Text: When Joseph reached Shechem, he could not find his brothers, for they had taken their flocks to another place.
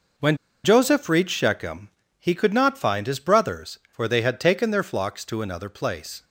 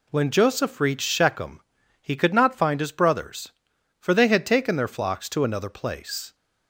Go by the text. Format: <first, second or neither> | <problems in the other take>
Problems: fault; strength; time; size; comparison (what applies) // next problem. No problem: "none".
second | pauses between "When" and "Joseph"; slight; at 0.3 s; 0.27 s long